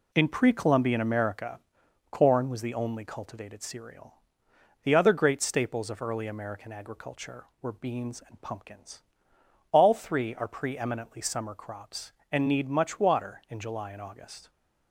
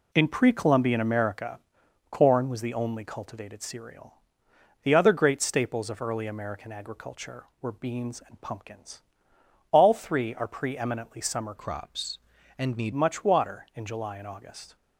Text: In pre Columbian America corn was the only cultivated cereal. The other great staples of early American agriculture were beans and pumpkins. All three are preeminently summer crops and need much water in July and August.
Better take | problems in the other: first | pauses between "America" and "corn"; noticeable; at 1.5 s; 0.52 s long; noticeable in the first // changes voice from "crops" to "need"; from 11.5 to 12.9 s; 1.4 s long

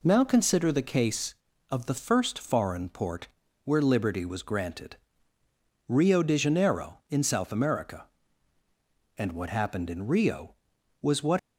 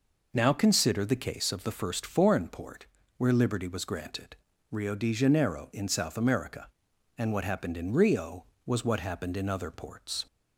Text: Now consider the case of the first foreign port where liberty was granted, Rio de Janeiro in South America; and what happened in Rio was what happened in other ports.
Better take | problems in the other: second | pauses between "port" and "where"; at 3.2 s; 0.38 s long; slight in the second // stops before "happened in other ports"; at 11.3 s

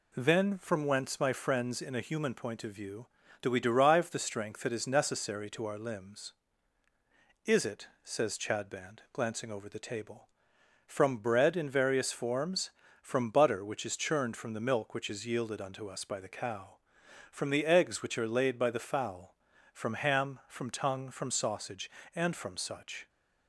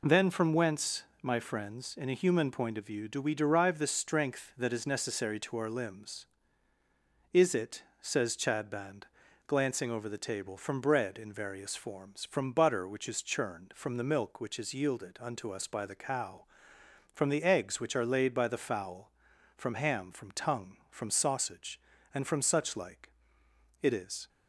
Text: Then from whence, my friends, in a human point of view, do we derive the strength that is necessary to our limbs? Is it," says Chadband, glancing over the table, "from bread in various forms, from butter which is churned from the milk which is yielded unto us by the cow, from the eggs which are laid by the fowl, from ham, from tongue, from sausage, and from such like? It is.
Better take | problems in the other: second | stops before "like It is"; at 23.0 s

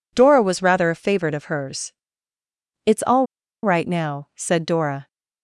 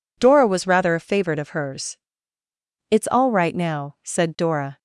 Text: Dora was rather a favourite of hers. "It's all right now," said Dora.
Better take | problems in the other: second | pauses between "all" and "right"; at 3.2 s; 0.37 s long

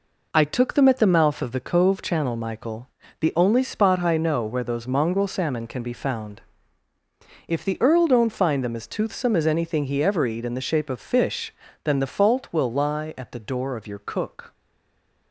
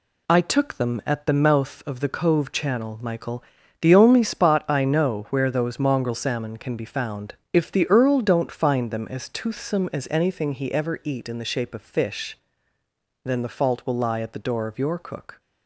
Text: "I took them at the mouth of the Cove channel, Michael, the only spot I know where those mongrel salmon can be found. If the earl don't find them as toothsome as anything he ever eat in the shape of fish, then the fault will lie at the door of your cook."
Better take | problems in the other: second | stays silent after the last word; slight; from 14.5 s on; 0.8 s long

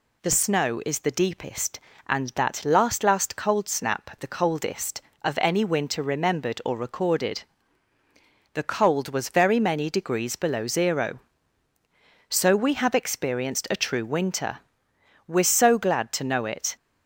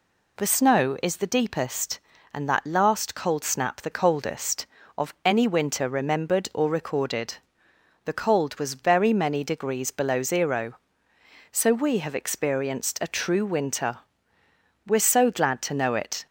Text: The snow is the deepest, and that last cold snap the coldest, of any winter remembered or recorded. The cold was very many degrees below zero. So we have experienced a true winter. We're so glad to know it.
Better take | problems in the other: second | says "last" twice; at 3.0 s

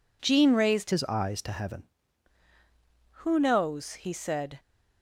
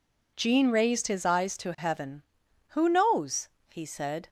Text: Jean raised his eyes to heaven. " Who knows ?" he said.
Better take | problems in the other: second | changes voice from "his" to "heaven"; from 0.9 to 1.8 s; 0.9 s long

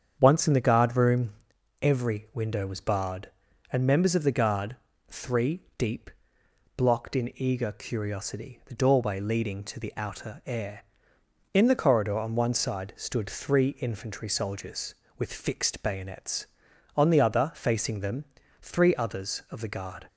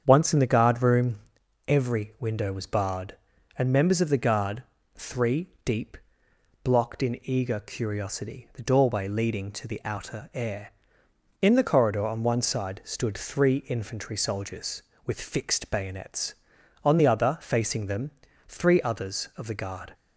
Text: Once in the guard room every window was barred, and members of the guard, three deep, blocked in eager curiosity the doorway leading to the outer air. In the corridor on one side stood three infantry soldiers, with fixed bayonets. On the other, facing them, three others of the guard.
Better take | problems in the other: neither | starts louder than the rest; strong; the same in both // pauses between "room" and "every"; noticeable; the same in both // pauses between "three" and "deep"; slight; the same in both

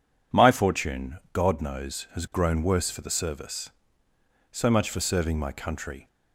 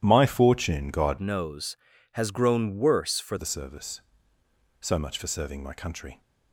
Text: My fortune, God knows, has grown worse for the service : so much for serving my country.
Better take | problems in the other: first | changes voice from "knows" to "for"; from 1.1 to 3.3 s; 2.2 s long

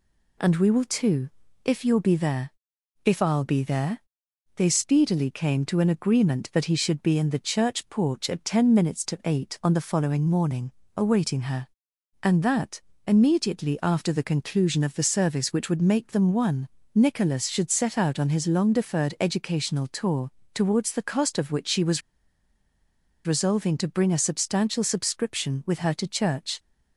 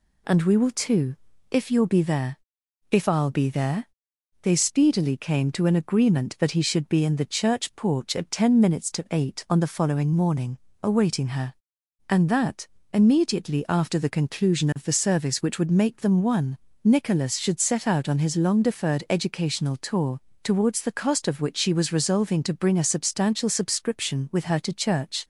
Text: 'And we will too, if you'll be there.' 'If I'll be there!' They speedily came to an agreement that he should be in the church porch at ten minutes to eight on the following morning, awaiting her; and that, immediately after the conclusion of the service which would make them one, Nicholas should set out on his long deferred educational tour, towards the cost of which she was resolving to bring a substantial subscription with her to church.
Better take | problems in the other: second | pauses between "was" and "resolving"; strong; at 22.0 s; 1.2 s long

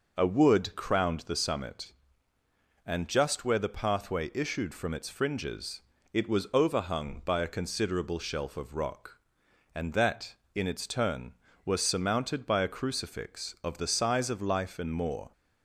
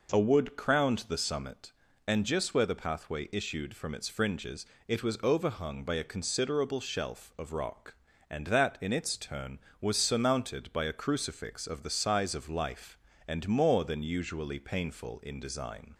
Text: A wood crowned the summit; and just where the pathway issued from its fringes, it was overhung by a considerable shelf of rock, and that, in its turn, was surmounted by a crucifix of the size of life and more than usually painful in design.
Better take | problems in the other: second | stops before "than usually painful in design"; at 15.3 s

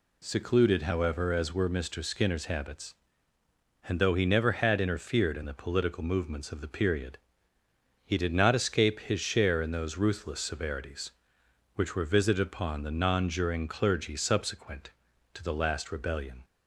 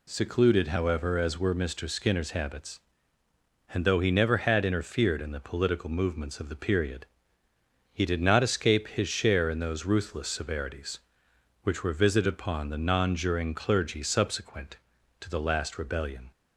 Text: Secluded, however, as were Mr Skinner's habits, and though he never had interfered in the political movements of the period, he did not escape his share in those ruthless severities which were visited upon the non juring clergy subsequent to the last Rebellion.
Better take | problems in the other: neither | none

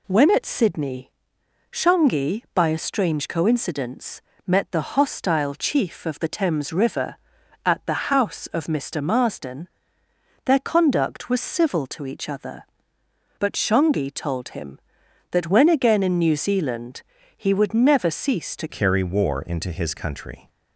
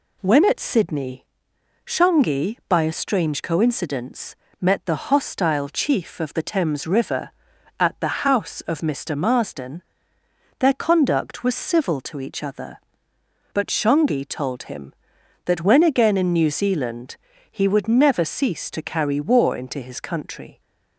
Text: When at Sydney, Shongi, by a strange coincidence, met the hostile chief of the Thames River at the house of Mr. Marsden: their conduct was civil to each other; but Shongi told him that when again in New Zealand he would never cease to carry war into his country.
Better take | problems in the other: second | pauses between "Zealand" and "he"; slight; at 17.0 s; 0.34 s long; slight in the second // changes voice at "carry"; from 18.6 s on; 1.8 s long

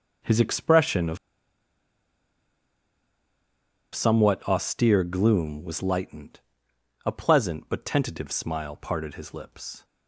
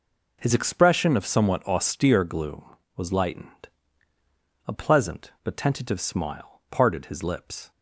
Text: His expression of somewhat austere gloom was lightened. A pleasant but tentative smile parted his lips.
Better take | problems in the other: second | pauses between "of" and "somewhat"; strong; at 1.1 s; 2.7 s long

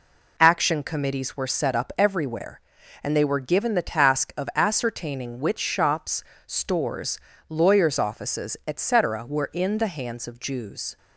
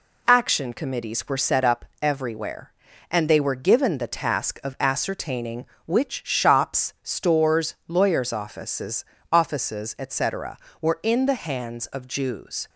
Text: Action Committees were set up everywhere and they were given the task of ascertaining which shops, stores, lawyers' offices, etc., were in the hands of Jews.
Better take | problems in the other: first | pauses between "up" and "everywhere"; slight; at 1.8 s; 0.16 s long // says "offices" twice; at 9.3 s

